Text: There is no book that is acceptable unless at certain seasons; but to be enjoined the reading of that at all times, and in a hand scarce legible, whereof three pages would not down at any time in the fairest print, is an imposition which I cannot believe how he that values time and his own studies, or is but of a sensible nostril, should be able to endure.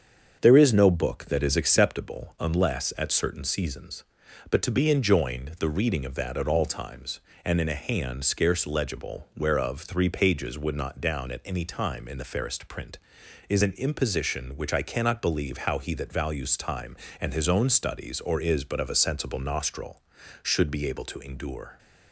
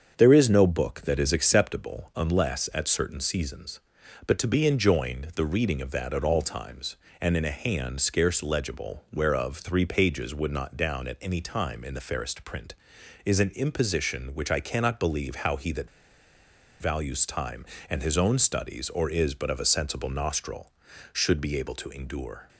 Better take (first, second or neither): first